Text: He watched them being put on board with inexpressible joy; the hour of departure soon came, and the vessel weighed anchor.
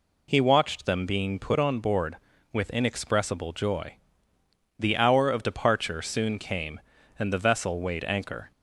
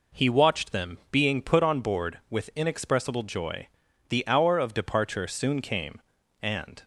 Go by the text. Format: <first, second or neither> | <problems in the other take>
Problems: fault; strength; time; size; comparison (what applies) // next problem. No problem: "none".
first | stops before "the vessel weighed anchor"; at 6.8 s